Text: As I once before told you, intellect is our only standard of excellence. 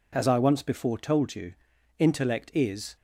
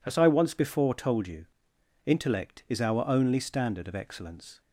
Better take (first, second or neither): second